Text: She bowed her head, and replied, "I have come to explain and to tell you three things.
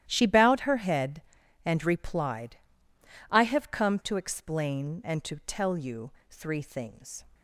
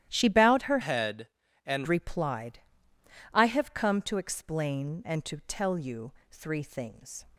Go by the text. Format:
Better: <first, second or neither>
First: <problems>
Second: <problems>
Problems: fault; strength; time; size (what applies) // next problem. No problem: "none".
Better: first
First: starts louder than the rest; strong; until 1.1 s; 12.5 dB // pauses between "you" and "three"; slight; at 6.0 s; 0.22 s long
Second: starts louder than the rest; strong; until 1.1 s; 12.5 dB // changes voice from "head" to "and"; from 0.8 to 1.8 s; 1.0 s long // pauses between "you" and "three"; slight; at 6.0 s; 0.22 s long